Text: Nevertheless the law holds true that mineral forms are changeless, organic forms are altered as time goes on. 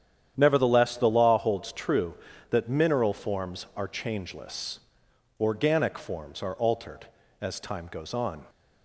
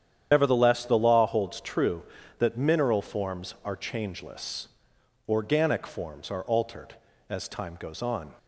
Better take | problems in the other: first | loses the start of "Nevertheless"; at 0.3 s; 70 ms // starts louder than the rest; strong; until 1.3 s; 9 dB; strong in the first

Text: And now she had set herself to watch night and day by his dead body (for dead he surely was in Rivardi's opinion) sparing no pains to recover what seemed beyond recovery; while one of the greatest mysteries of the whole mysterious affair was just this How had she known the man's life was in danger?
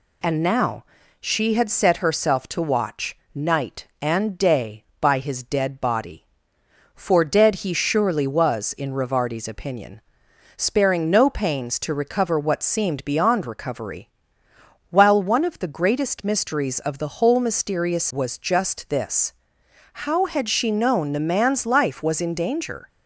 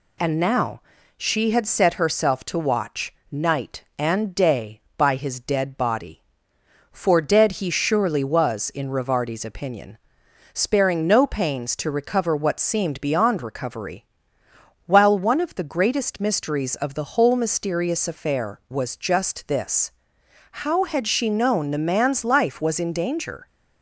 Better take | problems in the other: second | pauses between "now" and "she"; slight; at 0.8 s; 0.36 s long; slight in the second // pauses between "watch" and "night"; slight; at 3.1 s; 0.18 s long; slight in the second // skips "affair"; at 18.1 s // pauses between "this" and "How"; noticeable; at 19.3 s; 0.58 s long; noticeable in the second

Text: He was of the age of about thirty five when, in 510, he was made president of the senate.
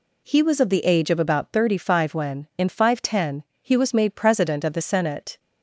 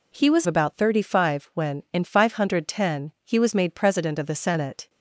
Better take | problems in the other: first | skips "of the age of"; at 0.4 s

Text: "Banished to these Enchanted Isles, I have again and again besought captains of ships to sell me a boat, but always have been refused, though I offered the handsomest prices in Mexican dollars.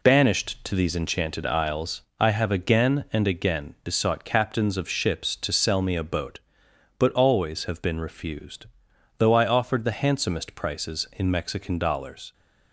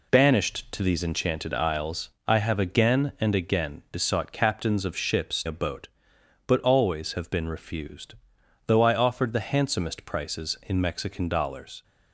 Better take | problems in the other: first | skips "to sell me"; at 5.4 s

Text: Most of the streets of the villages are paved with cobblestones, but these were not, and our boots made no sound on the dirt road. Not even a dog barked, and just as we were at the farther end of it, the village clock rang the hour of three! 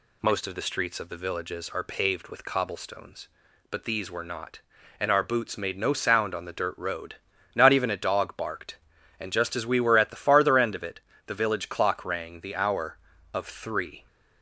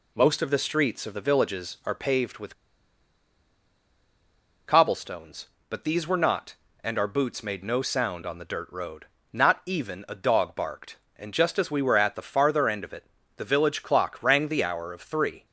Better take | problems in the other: first | pauses between "with" and "cobblestones"; strong; at 2.5 s; 2.1 s long

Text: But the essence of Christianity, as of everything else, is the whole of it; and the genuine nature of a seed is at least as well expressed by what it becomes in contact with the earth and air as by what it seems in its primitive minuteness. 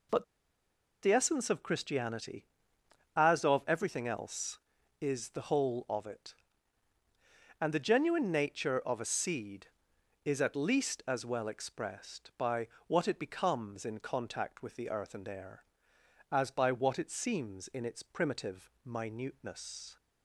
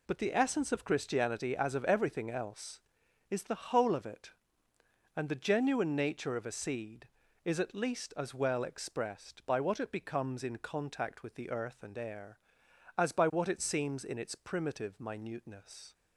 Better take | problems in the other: second | pauses between "But" and "the"; noticeable; at 0.2 s; 0.78 s long // pauses between "by" and "what"; slight; at 12.6 s; 0.18 s long

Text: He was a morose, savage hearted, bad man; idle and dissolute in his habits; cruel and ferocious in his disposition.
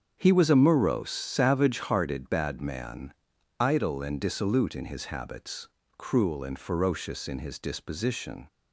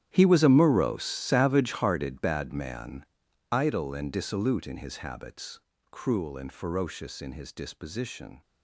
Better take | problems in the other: first | gets quieter; strong; throughout; 17 dB // starts louder than the rest; strong; until 1.1 s; 11 dB; strong in the first

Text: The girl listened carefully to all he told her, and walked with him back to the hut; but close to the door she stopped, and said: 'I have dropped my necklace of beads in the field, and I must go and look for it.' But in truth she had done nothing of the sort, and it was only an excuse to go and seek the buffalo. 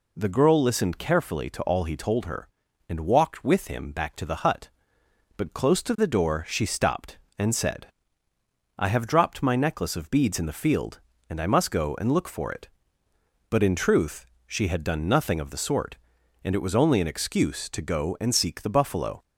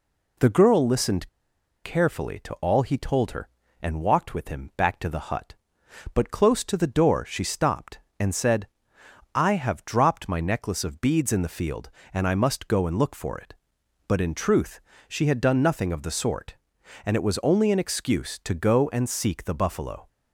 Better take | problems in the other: first | pauses between "listened" and "carefully"; noticeable; at 1.2 s; 0.54 s long // pauses between "truth" and "she"; slight; at 14.8 s; 0.26 s long; slight in the first

